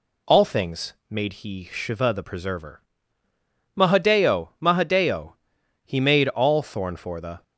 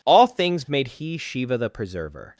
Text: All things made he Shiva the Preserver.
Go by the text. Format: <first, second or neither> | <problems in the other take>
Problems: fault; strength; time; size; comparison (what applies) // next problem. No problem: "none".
second | pauses between "things" and "made"; slight; at 0.9 s; 0.16 s long // goes on to say "Mahadeo Mahadeo He made all Thorn for the"; strong; from 3.7 s on; 3.6 s long